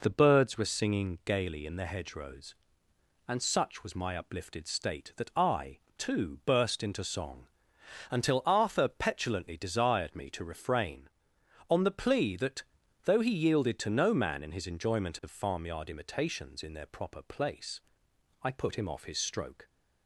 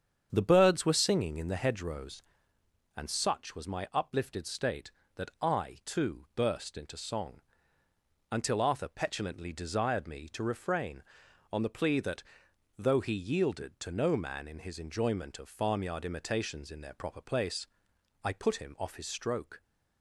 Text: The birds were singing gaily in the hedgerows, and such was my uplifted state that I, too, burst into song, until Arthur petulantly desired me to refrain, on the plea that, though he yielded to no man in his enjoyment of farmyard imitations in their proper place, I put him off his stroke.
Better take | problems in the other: first | starts louder than the rest; strong; until 1.3 s; 8 dB // skips "gaily"; at 1.3 s

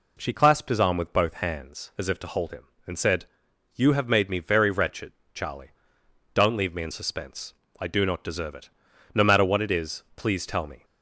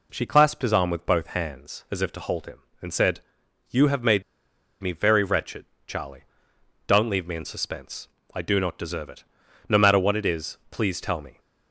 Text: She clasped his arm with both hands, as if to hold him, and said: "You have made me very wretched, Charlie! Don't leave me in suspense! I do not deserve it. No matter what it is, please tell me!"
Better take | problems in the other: first | pauses between "made" and "me"; noticeable; at 4.2 s; 0.60 s long

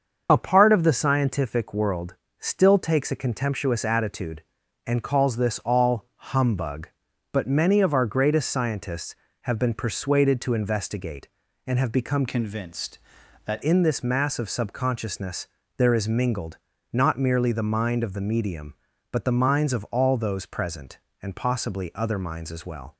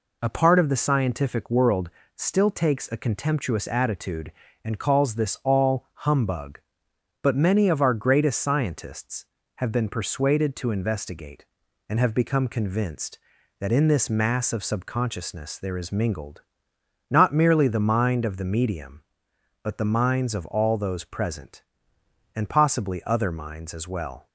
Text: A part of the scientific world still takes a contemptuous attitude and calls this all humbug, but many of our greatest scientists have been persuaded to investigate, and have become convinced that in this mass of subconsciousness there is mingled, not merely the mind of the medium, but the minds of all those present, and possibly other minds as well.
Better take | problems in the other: second | starts louder than the rest; until 1.3 s; 6.5 dB // pauses between "world" and "still"; slight; at 2.1 s; 0.24 s long; slight in the second // changes voice from "convinced" to "that"; from 12.2 to 13.6 s; 1.4 s long // pauses between "subconsciousness" and "there"; slight; at 15.4 s; 0.32 s long

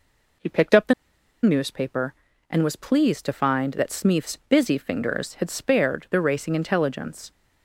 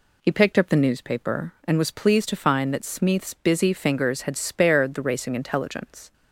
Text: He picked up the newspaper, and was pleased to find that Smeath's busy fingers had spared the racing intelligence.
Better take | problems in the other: second | pauses between "the" and "newspaper"; noticeable; at 0.9 s; 0.49 s long

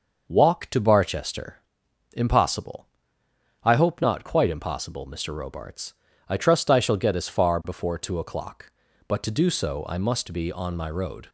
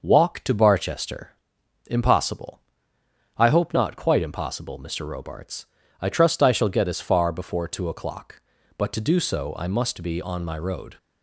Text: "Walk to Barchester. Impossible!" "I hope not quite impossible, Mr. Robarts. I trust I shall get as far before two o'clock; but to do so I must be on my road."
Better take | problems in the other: neither | none

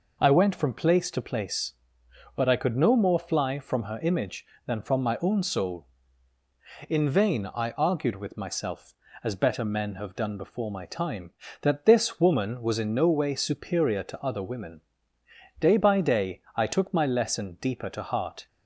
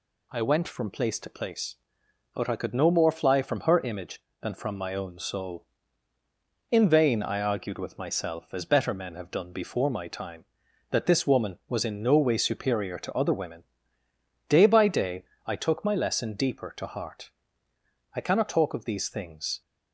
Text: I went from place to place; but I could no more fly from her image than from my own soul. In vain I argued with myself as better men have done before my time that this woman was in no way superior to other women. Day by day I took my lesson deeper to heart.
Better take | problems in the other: first | pauses between "day" and "I"; slight; at 15.2 s; 0.22 s long // goes on to say "I cannot talk of these things"; from 18.1 s on; 1.4 s long

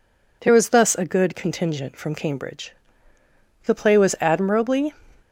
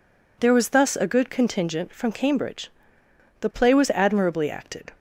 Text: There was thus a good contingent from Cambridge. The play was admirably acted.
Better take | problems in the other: second | stops before "acted"; at 5.2 s

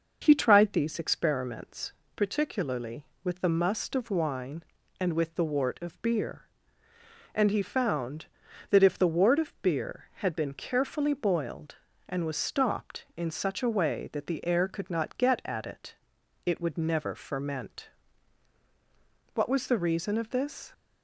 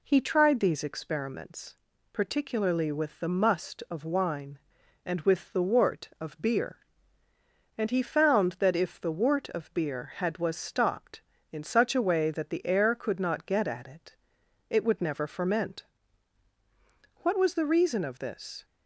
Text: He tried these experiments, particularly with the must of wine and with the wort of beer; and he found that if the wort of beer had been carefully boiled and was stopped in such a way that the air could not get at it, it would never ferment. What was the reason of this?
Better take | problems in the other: first | skips "been carefully boiled and"; at 10.3 s

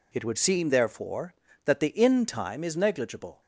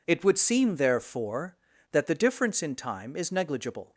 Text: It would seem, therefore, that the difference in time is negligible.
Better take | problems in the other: second | skips "difference"; at 1.8 s

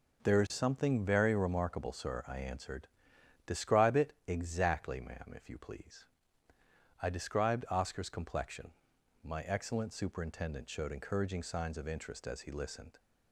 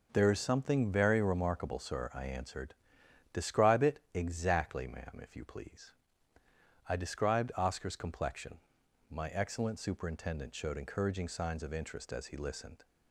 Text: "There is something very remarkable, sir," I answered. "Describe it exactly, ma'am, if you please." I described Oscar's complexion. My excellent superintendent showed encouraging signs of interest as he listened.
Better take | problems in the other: neither | pauses between "it" and "exactly"; slight; the same in both

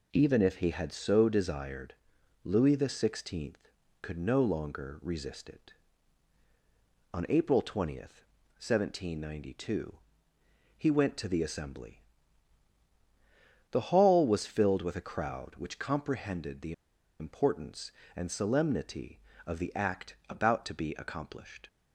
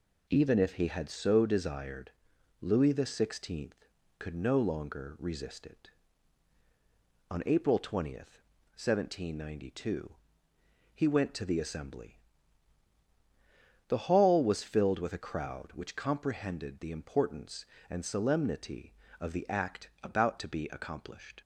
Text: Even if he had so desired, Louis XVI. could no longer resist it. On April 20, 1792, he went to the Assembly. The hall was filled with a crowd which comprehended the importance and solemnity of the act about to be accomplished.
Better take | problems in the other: second | pauses between "the" and "importance"; noticeable; at 16.7 s; 0.47 s long

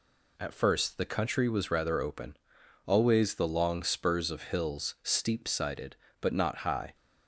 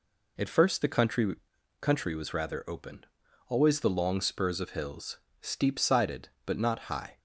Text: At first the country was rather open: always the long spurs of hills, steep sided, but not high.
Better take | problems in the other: first | says "country" twice; at 1.8 s

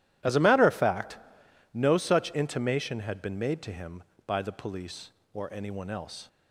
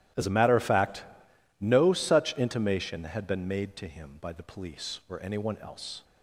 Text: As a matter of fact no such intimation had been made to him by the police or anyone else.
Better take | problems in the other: neither | starts louder than the rest; strong; the same in both // pauses between "fact" and "no"; noticeable; the same in both

